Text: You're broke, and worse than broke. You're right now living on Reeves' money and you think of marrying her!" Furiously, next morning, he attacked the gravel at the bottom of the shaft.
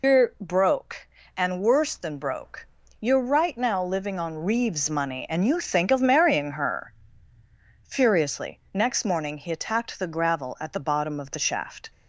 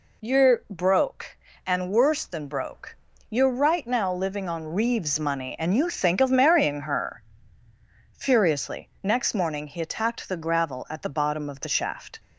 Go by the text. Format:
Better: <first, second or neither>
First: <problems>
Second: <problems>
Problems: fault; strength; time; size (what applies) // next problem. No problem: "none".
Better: second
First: loses the start of "You're"; at 0.0 s; 115 ms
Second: none